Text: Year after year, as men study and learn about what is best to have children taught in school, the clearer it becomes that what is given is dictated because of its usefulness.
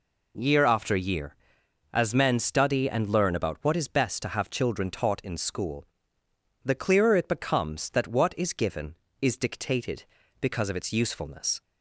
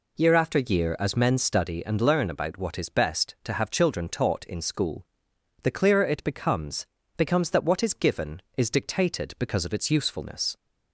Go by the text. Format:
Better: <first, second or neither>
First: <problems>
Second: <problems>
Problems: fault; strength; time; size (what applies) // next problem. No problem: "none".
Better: first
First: none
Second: says "becomes" twice; at 7.1 s